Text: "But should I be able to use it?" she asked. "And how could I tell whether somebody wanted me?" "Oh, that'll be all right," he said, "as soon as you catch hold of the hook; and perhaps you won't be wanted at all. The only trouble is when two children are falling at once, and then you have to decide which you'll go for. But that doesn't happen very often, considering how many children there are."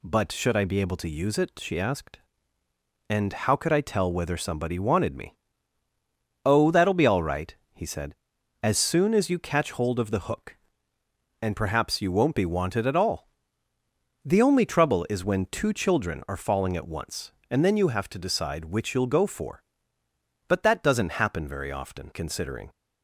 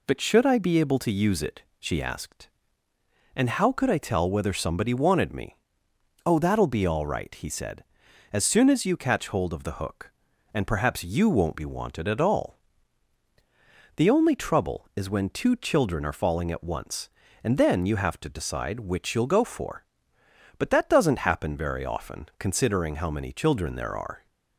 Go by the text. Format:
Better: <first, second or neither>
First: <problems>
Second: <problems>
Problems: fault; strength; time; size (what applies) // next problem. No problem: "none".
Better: second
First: stops before "how many children there are"; at 22.7 s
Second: none